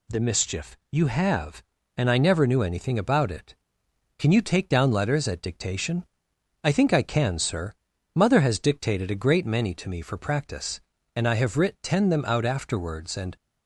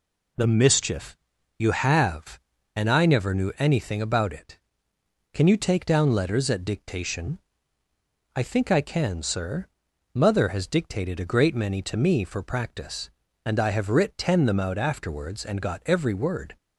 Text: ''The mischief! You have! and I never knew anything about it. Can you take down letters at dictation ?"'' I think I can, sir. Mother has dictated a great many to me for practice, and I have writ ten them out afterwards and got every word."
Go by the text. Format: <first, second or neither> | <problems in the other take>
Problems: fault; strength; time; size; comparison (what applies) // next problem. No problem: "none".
second | stops before "got every word"; at 13.3 s